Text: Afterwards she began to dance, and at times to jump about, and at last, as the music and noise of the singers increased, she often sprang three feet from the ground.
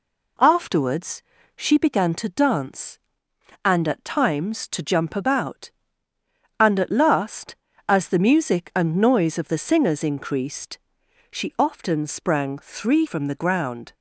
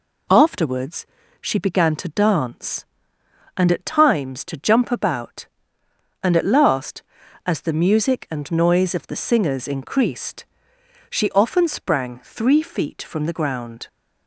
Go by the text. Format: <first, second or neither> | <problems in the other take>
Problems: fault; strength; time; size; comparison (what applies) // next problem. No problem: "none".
second | pauses between "Afterwards" and "she"; slight; at 1.2 s; 0.34 s long; slight in the second // skips "feet"; at 13.0 s